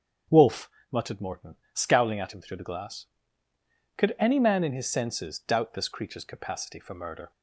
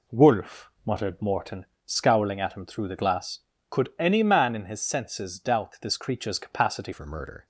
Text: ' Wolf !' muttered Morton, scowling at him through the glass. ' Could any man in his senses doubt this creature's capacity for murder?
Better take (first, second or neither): first